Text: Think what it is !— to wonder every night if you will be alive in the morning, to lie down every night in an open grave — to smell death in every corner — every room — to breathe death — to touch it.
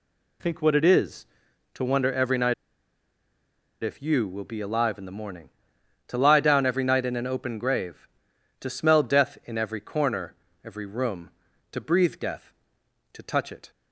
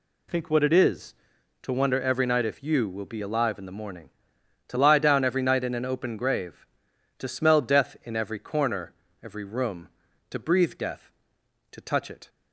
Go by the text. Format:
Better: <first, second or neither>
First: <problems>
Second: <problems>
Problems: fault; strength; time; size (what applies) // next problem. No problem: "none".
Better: second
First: pauses between "night" and "if"; strong; at 2.5 s; 1.2 s long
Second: none